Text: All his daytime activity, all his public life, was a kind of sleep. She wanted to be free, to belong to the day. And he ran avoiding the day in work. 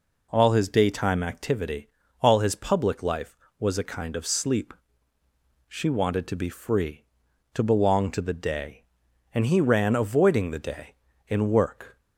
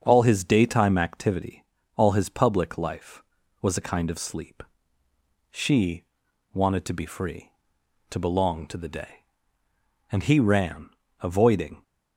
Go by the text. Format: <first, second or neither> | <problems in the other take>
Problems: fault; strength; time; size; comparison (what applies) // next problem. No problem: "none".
first | starts louder than the rest; until 1.0 s; 7 dB // pauses between "She" and "wanted"; noticeable; at 6.0 s; 0.50 s long // pauses between "ran" and "avoiding"; slight; at 10.8 s; 0.32 s long // stops before "the day in work"; at 11.8 s